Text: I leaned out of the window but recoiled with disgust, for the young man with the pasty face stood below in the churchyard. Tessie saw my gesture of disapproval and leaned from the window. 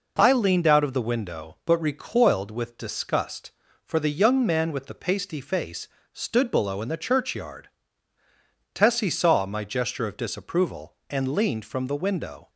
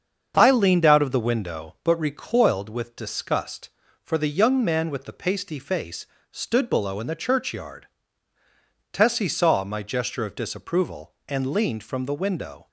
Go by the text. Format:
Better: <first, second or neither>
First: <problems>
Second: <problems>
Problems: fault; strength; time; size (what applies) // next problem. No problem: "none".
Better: first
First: pauses between "face" and "stood"; slight; at 5.8 s; 0.24 s long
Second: starts louder than the rest; until 1.9 s; 7 dB // pauses between "face" and "stood"; slight; at 6.0 s; 0.24 s long